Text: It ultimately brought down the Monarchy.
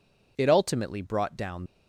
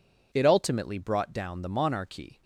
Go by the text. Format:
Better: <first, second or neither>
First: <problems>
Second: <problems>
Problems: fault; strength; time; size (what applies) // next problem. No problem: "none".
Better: second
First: stops before "the Monarchy"; at 1.6 s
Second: none